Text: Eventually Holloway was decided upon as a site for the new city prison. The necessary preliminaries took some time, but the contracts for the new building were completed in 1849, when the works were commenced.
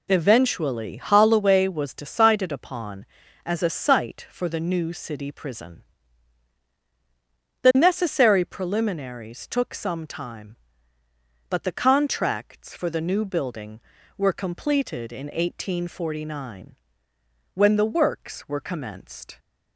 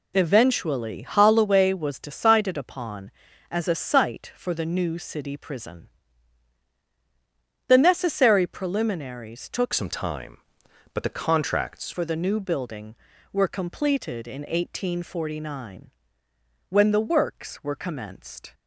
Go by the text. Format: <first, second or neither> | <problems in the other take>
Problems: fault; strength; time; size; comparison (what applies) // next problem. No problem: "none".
first | changes voice from "some" to "contracts"; from 9.7 to 11.9 s; 2.2 s long